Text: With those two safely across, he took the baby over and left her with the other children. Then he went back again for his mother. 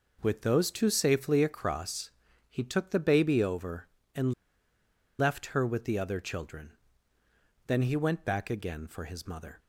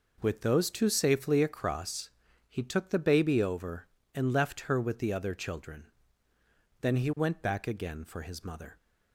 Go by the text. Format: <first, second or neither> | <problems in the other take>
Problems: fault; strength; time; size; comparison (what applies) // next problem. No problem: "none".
second | pauses between "and" and "left"; noticeable; at 4.3 s; 0.85 s long